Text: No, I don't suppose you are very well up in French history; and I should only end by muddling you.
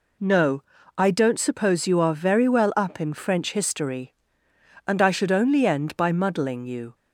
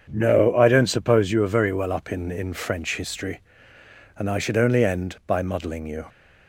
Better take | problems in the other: first | starts louder than the rest; until 1.1 s; 7 dB // says "in" twice; at 2.3 s

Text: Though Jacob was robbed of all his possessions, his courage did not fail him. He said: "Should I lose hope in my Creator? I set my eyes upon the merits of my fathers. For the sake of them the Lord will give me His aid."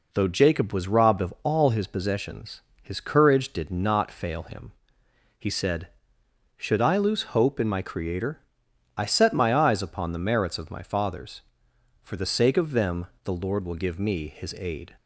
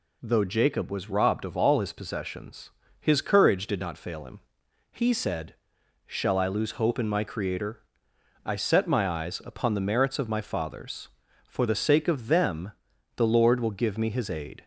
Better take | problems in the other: first | says "Shall" for "Should"; at 6.0 s // pauses between "them" and "the"; noticeable; at 12.7 s; 0.46 s long; slight in the first

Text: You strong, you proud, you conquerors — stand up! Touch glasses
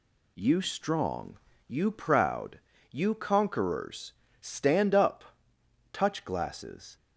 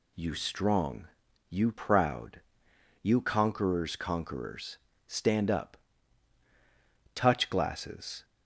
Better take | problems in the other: first | says "conquerors" twice; at 3.9 s

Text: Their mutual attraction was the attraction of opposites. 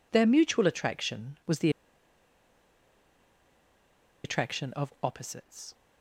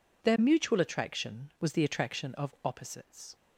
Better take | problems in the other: second | pauses between "the" and "attraction"; strong; at 1.6 s; 2.5 s long

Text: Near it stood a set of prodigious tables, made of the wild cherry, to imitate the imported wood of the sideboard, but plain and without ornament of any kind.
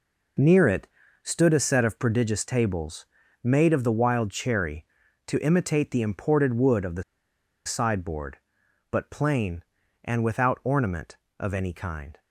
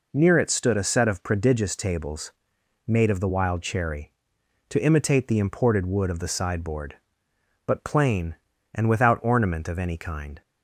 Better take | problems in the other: second | pauses between "it" and "stood"; at 0.8 s; 0.38 s long // pauses between "the" and "sideboard"; noticeable; at 7.0 s; 0.62 s long

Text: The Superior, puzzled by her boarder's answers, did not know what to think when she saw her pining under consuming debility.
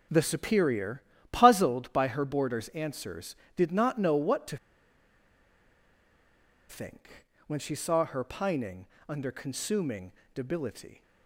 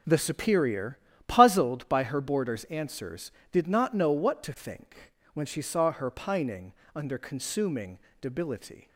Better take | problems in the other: second | pauses between "to" and "think"; strong; at 4.5 s; 2.1 s long // pauses between "think" and "when"; slight; at 7.2 s; 0.22 s long; slight in the second // pauses between "pining" and "under"; slight; at 8.8 s; 0.20 s long; slight in the second // pauses between "consuming" and "debility"; slight; at 10.1 s; 0.22 s long; slight in the second

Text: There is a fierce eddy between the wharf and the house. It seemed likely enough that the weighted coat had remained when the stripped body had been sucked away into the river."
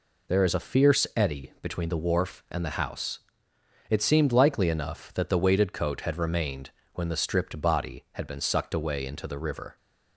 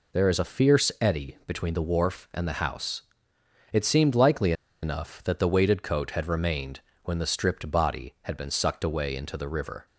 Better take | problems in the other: first | pauses between "likely" and "enough"; slight; at 4.5 s; 0.30 s long // pauses between "remained" and "when"; slight; at 6.7 s; 0.24 s long; slight in the first

